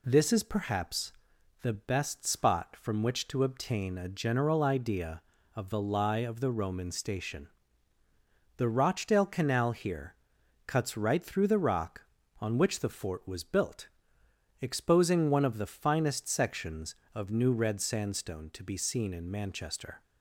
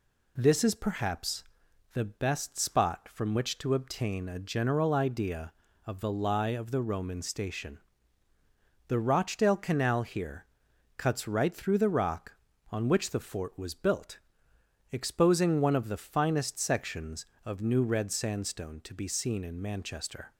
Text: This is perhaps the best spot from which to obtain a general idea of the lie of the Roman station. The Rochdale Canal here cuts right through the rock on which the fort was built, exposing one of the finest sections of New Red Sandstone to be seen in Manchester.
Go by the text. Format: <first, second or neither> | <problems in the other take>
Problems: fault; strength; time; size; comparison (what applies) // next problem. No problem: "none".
neither | pauses between "perhaps" and "the"; noticeable; the same in both // pauses between "here" and "cuts"; noticeable; the same in both